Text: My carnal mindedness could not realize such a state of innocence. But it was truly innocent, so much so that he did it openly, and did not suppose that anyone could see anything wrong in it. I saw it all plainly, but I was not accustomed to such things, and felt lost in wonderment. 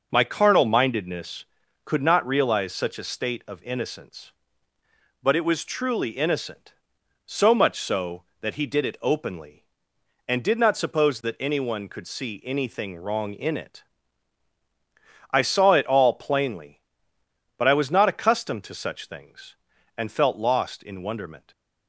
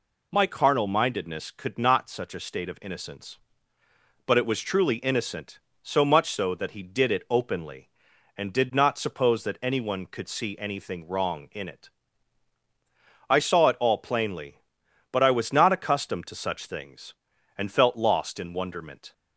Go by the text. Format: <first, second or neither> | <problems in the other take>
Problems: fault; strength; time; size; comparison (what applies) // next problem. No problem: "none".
first | skips "realize"; at 2.0 s